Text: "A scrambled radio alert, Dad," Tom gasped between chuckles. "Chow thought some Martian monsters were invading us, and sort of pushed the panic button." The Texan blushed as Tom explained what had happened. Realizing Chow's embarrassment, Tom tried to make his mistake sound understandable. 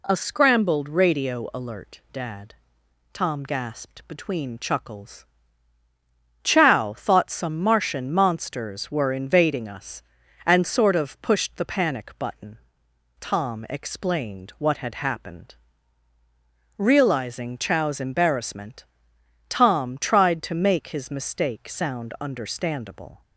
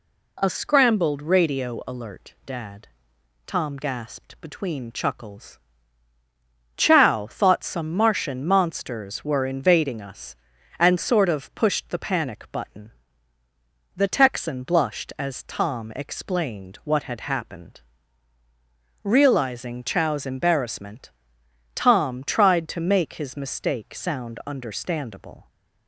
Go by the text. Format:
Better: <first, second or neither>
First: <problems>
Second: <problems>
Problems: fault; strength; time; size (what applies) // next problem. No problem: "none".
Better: second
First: skips "The Texan blushed as"; at 12.8 s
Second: none